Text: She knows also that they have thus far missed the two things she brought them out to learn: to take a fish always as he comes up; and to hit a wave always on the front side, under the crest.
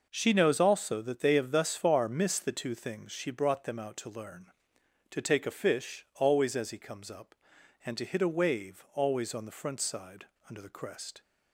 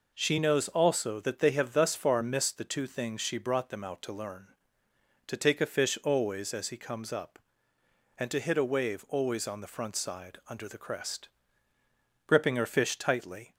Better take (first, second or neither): first